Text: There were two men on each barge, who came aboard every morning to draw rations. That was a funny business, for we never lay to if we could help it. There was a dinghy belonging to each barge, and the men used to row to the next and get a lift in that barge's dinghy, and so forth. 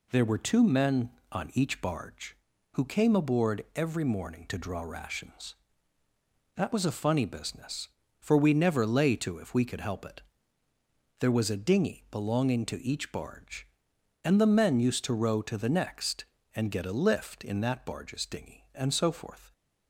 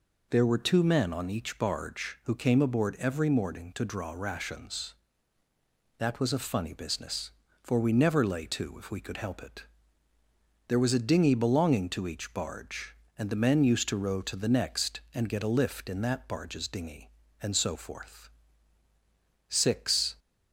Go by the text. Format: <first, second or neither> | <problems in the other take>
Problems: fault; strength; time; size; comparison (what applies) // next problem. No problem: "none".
first | goes on to say "Six"; noticeable; from 19.4 s on; 0.70 s long